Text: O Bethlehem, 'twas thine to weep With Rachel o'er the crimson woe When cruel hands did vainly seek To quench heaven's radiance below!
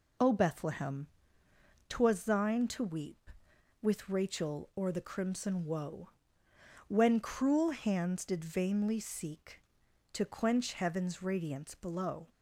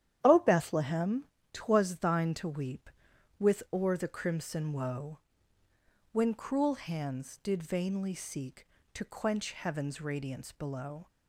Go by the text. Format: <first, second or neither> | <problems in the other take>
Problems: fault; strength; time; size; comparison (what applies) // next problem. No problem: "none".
first | starts louder than the rest; strong; until 1.2 s; 10.5 dB // skips "Rachel"; at 3.6 s // pauses between "woe" and "When"; noticeable; at 5.1 s; 0.94 s long; noticeable in the first